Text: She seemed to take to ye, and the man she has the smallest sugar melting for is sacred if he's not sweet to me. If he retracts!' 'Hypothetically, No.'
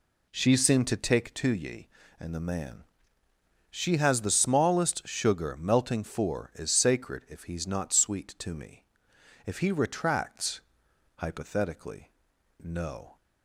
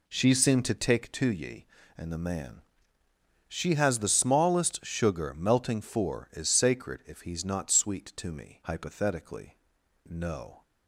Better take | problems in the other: first | pauses between "man" and "she"; noticeable; at 2.6 s; 0.86 s long; noticeable in the first // skips "If he retracts"; at 8.6 s

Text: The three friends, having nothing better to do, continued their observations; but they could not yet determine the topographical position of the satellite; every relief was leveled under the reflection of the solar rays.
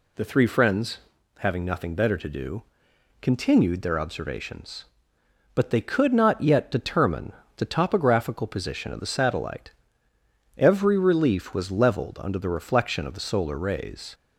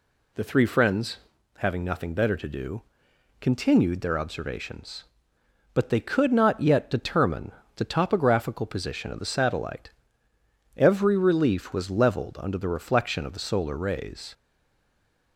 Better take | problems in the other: first | pauses between "determine" and "the"; slight; at 7.5 s; 0.24 s long; slight in the first // stays silent after the last word; from 14.3 s on; 1.0 s long

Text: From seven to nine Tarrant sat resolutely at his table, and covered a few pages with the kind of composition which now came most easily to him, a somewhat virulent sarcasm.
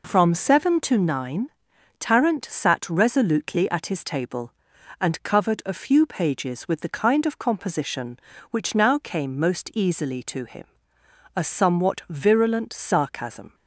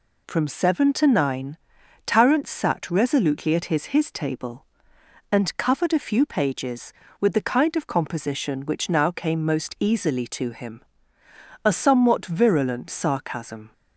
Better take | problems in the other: first | pauses between "nine" and "Tarrant"; noticeable; at 1.5 s; 0.50 s long; noticeable in the first // says "his" twice; at 3.8 s

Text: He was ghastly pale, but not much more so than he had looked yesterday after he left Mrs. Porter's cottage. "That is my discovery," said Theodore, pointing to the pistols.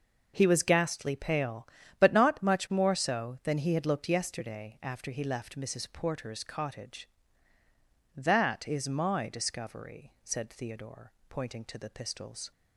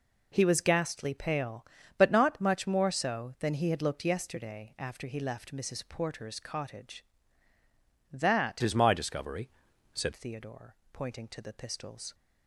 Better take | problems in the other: first | changes voice from "is" to "said"; from 8.6 to 10.1 s; 1.5 s long

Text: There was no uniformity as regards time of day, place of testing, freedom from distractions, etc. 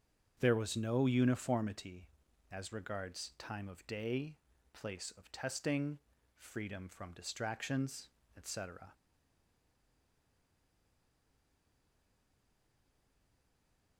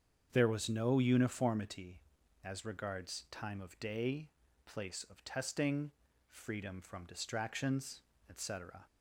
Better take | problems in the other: second | starts louder than the rest; strong; until 1.4 s; 7.5 dB; strong in the second // stays silent after the last word; strong; from 8.9 s on; 5.0 s long

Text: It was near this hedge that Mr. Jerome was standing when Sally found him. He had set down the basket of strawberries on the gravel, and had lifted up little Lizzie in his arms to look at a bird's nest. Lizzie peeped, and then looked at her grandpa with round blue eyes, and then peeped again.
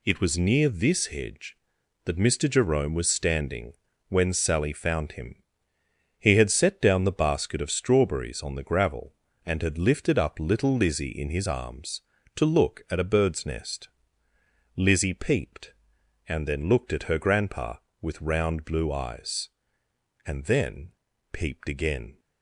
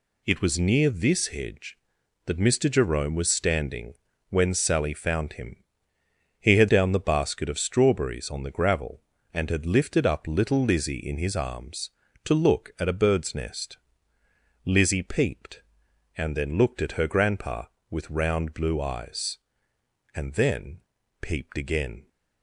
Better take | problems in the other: first | pauses between "standing" and "when"; slight; at 3.9 s; 0.34 s long; slight in the first // skips "set"; at 6.6 s // pauses between "then" and "peeped"; at 20.7 s; 0.42 s long; also in the first

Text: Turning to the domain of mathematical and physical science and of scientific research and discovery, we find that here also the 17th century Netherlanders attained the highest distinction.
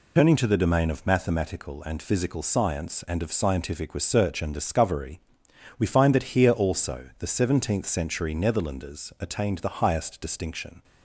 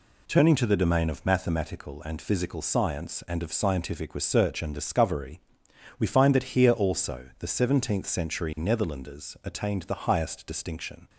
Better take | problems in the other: second | loses the start of "Turning"; at 0.1 s; 75 ms

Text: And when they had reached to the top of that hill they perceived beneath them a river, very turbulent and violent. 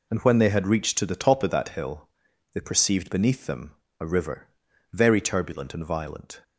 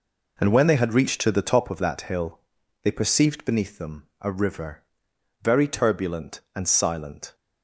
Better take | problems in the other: first | pauses between "hill" and "they"; at 2.3 s; 0.44 s long; also in the first // pauses between "them" and "a"; slight; at 4.0 s; 0.18 s long; slight in the first // says "silent" for "violent"; at 6.6 s

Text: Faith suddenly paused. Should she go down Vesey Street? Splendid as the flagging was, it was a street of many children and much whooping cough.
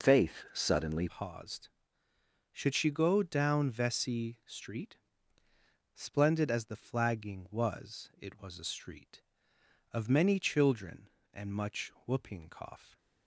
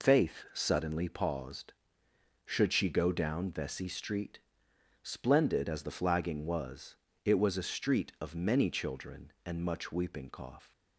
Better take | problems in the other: second | changes voice at "paused"; from 1.0 s on; 11.9 s long

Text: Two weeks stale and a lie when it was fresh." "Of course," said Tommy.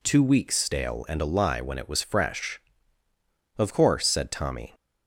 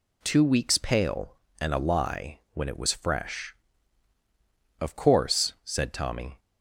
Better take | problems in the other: first | says "pale" for "stale"; at 0.7 s

